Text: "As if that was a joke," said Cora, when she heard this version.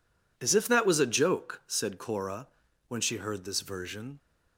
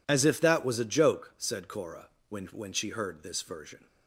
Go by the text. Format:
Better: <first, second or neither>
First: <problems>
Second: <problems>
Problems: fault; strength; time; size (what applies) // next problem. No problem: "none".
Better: first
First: none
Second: says "when" twice; at 2.4 s